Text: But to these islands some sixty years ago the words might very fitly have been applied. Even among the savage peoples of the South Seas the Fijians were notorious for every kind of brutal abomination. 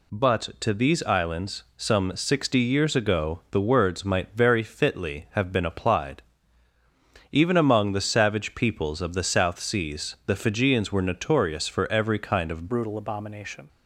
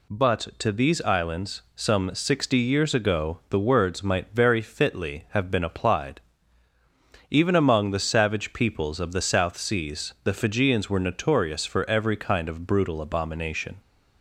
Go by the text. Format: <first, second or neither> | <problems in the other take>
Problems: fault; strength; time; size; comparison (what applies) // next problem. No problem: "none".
second | changes voice at "brutal"; from 12.6 s on; 1.0 s long